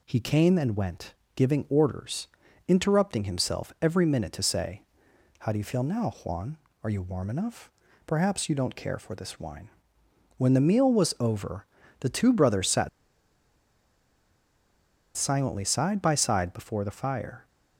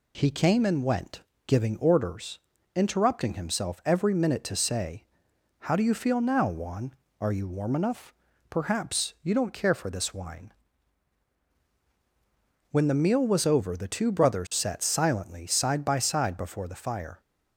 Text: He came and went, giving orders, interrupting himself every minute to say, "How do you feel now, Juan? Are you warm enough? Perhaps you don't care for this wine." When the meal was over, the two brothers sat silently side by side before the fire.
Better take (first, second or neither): second